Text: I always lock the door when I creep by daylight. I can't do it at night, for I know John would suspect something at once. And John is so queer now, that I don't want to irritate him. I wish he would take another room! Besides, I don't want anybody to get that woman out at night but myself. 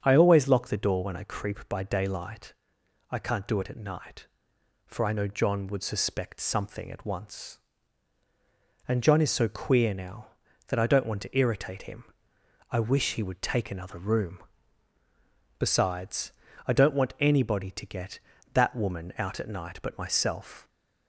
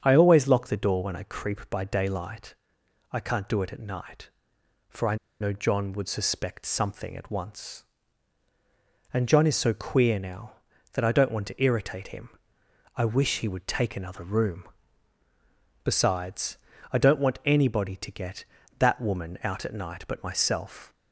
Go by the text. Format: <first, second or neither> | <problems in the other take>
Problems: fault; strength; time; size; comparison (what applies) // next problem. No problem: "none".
first | starts louder than the rest; strong; until 1.0 s; 7.5 dB; strong in the first // pauses between "I" and "know"; slight; at 5.1 s; 0.25 s long